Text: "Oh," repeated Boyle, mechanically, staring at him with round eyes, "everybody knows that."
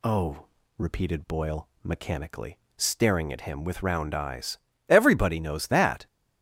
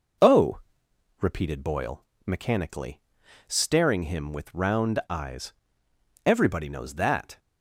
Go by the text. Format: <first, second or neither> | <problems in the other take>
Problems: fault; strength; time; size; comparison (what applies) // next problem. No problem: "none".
first | skips "at"; at 4.0 s